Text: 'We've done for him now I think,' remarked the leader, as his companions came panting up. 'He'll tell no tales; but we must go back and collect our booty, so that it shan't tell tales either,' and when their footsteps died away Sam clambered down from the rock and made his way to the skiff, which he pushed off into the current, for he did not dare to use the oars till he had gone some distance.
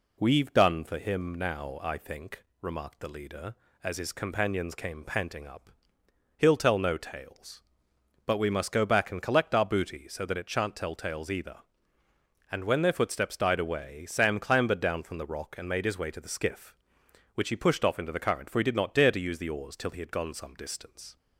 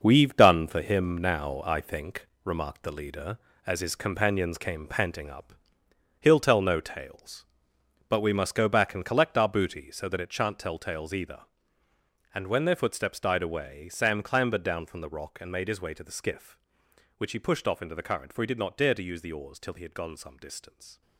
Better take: first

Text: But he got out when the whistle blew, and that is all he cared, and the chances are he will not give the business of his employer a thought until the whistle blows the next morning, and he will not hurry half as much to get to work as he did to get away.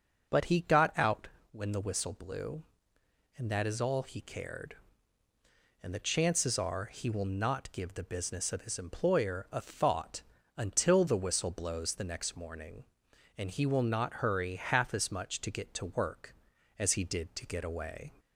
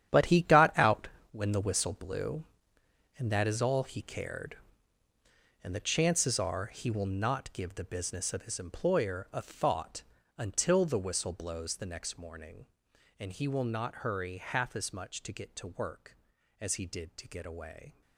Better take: first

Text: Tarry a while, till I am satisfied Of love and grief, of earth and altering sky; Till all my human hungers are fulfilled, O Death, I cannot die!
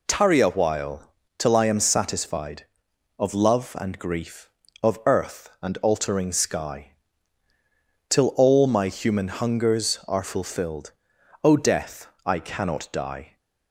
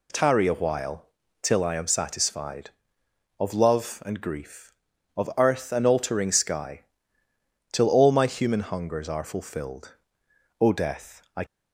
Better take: first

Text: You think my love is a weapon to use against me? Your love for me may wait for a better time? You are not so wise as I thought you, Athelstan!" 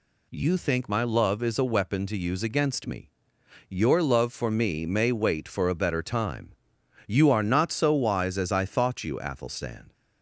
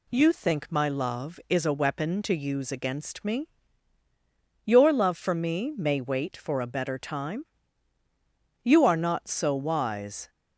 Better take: first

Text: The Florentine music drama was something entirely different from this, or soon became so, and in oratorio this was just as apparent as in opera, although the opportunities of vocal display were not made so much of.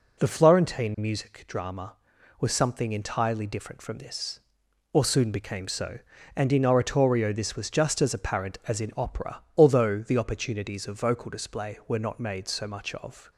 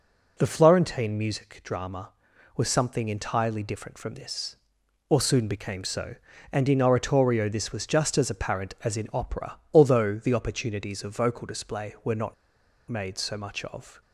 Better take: first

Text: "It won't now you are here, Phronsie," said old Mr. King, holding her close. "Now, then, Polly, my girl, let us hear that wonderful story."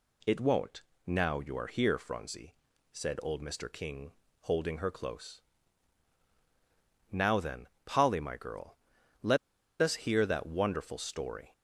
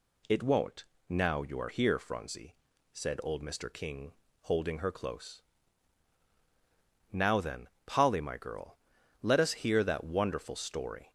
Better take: second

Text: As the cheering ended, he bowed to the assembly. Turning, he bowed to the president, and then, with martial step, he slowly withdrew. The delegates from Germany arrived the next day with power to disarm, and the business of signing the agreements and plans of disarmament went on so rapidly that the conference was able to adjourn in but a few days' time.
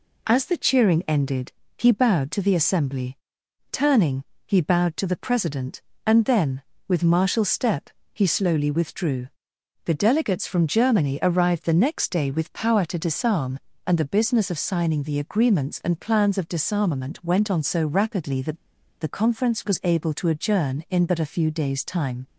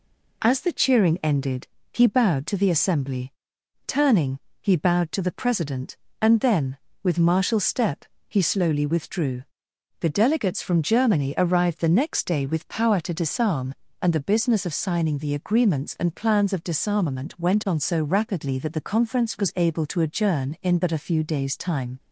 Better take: second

